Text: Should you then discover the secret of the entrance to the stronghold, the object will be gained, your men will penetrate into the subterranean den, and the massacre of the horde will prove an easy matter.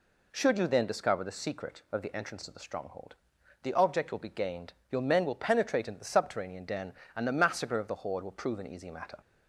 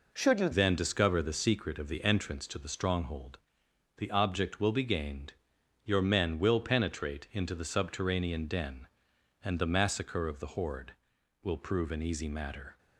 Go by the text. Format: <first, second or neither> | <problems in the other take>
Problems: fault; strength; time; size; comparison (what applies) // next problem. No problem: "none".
first | changes voice at "then"; from 0.5 s on; 12.2 s long